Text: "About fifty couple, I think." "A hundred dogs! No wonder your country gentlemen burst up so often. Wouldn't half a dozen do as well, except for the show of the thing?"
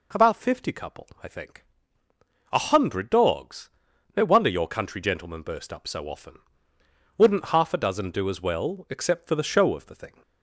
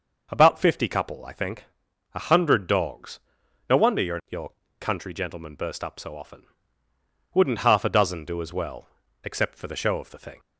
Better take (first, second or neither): first